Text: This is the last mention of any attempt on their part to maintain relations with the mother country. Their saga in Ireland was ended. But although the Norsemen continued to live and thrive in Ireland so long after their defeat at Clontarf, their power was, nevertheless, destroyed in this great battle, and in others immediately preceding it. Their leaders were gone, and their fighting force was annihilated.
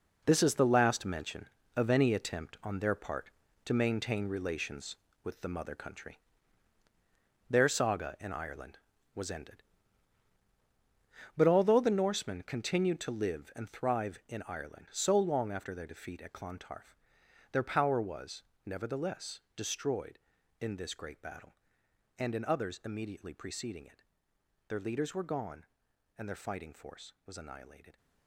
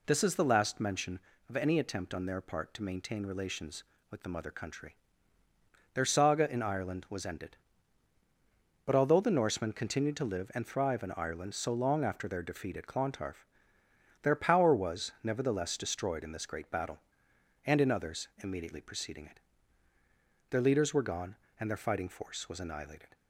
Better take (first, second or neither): second